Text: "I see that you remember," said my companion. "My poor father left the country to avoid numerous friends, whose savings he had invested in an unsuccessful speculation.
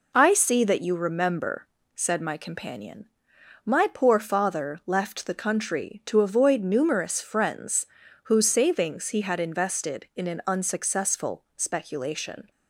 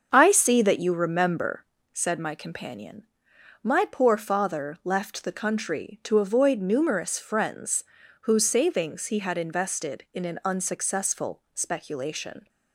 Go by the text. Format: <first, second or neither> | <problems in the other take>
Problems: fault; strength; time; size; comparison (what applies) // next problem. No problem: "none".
first | starts louder than the rest; until 1.7 s; 6.5 dB